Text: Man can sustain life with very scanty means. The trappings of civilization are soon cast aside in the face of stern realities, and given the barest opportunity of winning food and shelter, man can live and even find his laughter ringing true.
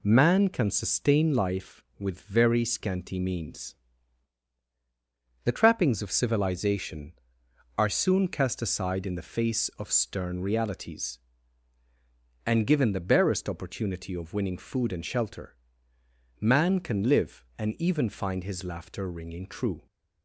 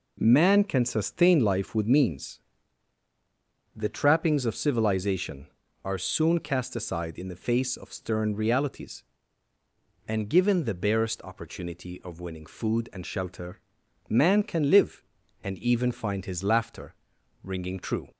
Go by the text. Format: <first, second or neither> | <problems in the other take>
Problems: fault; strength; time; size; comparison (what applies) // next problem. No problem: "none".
first | skips "very scanty"; at 1.8 s // pauses between "laughter" and "ringing"; noticeable; at 16.9 s; 0.50 s long